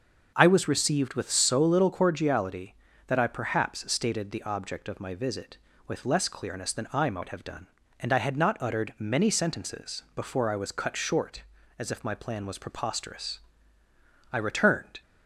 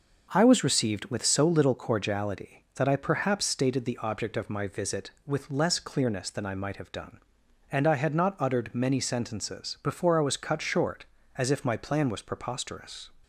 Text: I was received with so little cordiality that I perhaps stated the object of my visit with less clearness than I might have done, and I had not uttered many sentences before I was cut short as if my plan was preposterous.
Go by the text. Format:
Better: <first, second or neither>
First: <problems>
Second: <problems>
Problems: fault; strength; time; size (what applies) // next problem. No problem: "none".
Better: second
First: starts louder than the rest; until 1.3 s; 6.5 dB // goes on to say "I returned"; noticeable; from 14.3 s on; 0.70 s long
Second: none